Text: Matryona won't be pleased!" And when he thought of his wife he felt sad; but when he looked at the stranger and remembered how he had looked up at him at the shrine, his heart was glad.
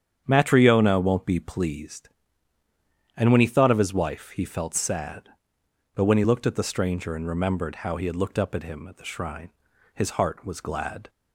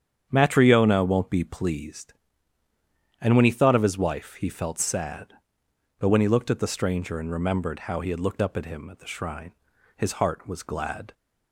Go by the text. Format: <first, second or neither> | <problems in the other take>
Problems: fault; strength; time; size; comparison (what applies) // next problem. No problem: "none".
neither | starts louder than the rest; strong; the same in both